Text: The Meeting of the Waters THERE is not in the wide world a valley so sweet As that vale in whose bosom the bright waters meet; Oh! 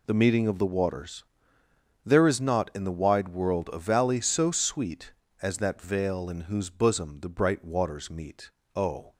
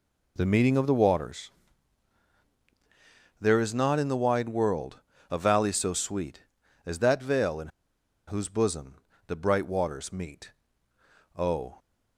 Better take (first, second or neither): first